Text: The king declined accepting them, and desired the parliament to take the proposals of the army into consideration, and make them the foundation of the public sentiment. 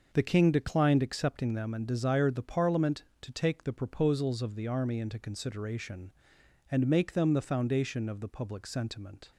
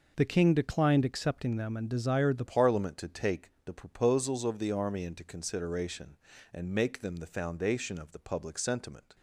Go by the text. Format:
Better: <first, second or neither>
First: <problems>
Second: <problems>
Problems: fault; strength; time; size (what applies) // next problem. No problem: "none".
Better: first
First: none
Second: changes voice at "parliament"; from 2.4 s on; 6.7 s long // pauses between "take" and "the"; slight; at 3.4 s; 0.16 s long